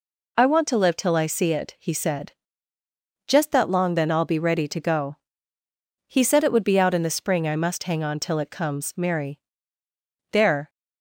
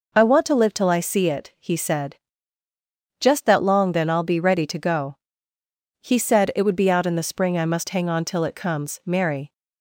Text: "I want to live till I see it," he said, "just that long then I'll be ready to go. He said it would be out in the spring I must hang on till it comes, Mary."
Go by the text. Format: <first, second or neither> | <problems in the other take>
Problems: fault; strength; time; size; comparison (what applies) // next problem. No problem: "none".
second | goes on to say "There"; slight; from 10.3 s on; 0.38 s long